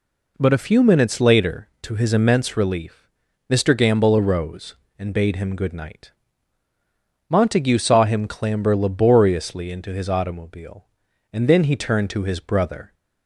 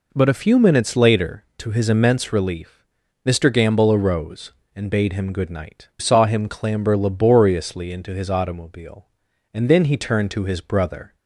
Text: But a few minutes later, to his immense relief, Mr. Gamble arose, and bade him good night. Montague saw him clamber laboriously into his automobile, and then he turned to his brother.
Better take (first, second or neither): first